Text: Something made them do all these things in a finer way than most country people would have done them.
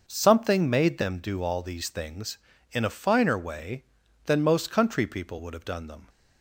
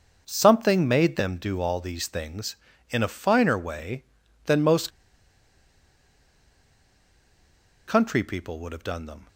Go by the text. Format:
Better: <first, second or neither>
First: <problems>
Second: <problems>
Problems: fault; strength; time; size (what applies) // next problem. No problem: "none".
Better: first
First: starts louder than the rest; noticeable; until 1.0 s; 6 dB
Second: starts louder than the rest; until 1.2 s; 6 dB // pauses between "most" and "country"; strong; at 4.8 s; 2.9 s long